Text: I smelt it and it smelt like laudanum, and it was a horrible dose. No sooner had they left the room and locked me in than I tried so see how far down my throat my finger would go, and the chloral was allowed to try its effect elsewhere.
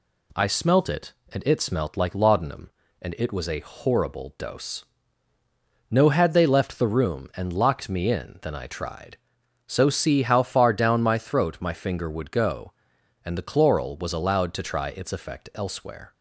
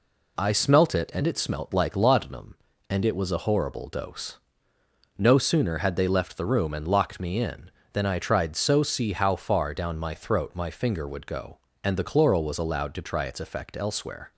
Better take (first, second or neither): second